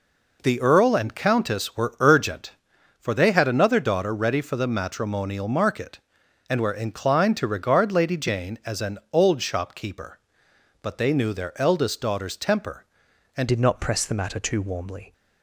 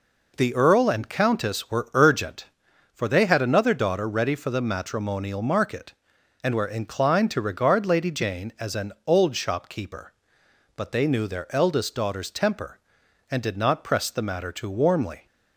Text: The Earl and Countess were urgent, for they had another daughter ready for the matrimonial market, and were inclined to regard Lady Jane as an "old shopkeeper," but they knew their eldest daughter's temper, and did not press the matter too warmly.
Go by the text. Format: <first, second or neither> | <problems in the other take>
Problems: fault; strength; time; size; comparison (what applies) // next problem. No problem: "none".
second | changes voice at "did"; from 13.4 s on; 1.7 s long